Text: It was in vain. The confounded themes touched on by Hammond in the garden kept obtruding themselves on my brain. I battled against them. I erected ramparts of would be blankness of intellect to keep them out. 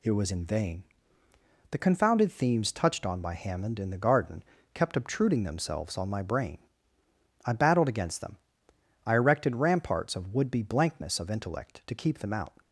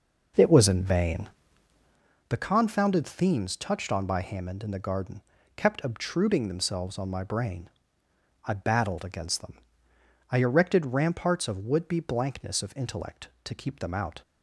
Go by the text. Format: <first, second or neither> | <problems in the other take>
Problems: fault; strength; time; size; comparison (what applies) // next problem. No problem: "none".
first | starts louder than the rest; noticeable; until 2.0 s; 5.5 dB // pauses between "garden" and "kept"; slight; at 5.2 s; 0.36 s long; slight in the first